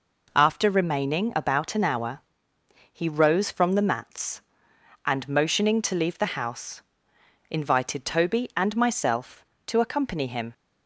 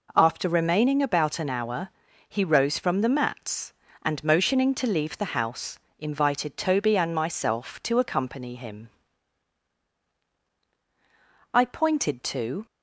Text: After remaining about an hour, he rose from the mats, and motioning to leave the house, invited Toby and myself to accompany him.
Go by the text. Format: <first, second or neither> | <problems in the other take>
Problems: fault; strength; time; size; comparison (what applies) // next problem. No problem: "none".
first | goes on to say "I pointed to"; noticeable; from 11.5 s on; 1.1 s long